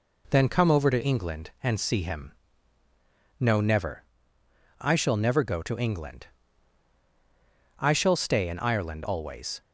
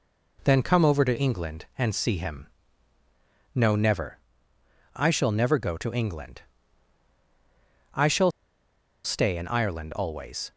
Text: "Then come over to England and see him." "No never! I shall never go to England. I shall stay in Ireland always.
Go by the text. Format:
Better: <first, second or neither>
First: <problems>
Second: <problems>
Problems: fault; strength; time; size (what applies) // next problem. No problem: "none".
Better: first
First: none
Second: pauses between "shall" and "stay"; noticeable; at 8.3 s; 0.74 s long